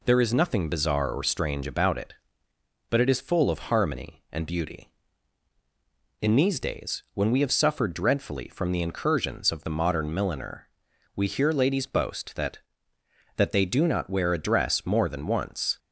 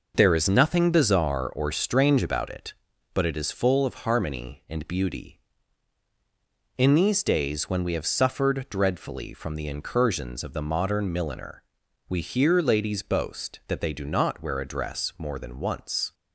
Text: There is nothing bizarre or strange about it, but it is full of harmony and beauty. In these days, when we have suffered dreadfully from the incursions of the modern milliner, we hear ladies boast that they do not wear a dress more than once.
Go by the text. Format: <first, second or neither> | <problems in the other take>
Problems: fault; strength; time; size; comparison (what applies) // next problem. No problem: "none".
second | says "that" twice; at 13.3 s